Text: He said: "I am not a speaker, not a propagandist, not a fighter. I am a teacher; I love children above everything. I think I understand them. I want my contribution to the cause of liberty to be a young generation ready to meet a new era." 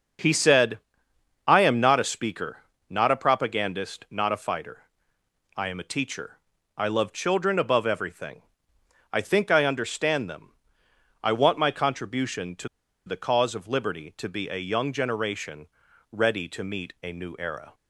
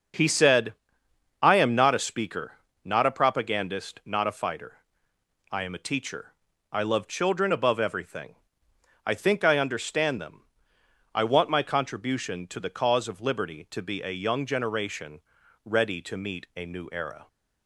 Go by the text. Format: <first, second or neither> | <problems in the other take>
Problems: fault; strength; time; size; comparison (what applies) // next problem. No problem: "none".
second | starts louder than the rest; until 1.8 s; 6 dB; noticeable in the second // pauses between "to" and "the"; at 12.6 s; 0.38 s long // pauses between "generation" and "ready"; at 15.6 s; 0.44 s long; also in the second